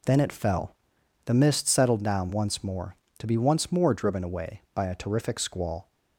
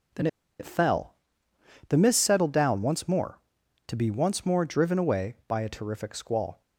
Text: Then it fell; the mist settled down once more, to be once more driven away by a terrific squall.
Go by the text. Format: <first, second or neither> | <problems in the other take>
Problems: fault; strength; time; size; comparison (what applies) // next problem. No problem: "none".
first | pauses between "Then" and "it"; slight; at 0.2 s; 0.32 s long